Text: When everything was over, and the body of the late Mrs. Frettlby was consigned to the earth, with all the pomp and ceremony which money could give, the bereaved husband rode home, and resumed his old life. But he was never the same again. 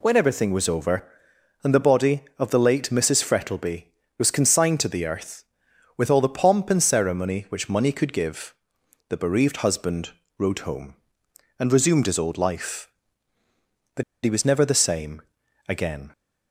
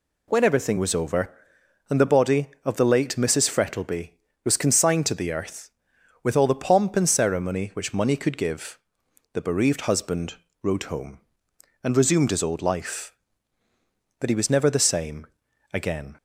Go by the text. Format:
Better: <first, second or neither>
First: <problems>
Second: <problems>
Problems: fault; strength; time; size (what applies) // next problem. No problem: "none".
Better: second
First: pauses between "husband" and "rode"; slight; at 10.0 s; 0.30 s long // pauses between "But" and "he"; slight; at 14.0 s; 0.21 s long // pauses between "same" and "again"; at 15.2 s; 0.44 s long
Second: pauses between "husband" and "rode"; slight; at 10.3 s; 0.30 s long // pauses between "same" and "again"; at 15.2 s; 0.44 s long